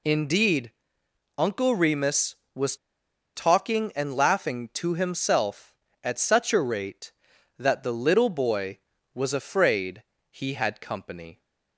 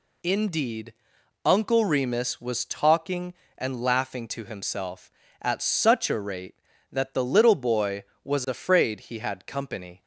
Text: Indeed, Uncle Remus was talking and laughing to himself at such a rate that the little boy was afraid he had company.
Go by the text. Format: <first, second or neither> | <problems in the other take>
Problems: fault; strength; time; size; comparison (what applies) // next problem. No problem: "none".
second | pauses between "was" and "talking"; noticeable; at 2.7 s; 0.60 s long // pauses between "afraid" and "he"; slight; at 10.0 s; 0.26 s long